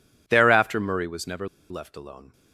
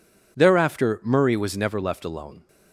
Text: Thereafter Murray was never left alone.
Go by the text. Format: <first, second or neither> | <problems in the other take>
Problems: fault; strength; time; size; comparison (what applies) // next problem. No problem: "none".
second | pauses between "never" and "left"; slight; at 1.4 s; 0.24 s long